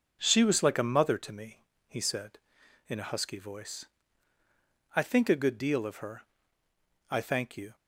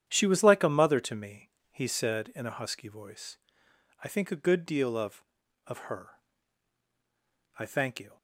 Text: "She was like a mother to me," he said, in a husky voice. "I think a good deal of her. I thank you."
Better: first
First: none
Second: starts louder than the rest; strong; until 1.0 s; 9.5 dB // says "of" twice; at 5.6 s

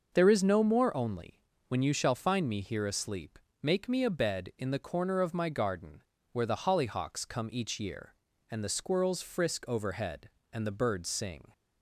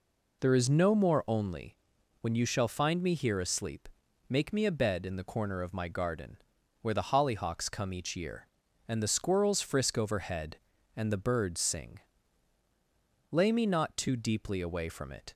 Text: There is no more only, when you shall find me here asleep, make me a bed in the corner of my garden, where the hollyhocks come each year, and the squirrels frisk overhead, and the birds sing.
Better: first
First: none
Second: goes on to say "Lay me not too deeply away from it"; strong; from 13.3 s on; 2.0 s long

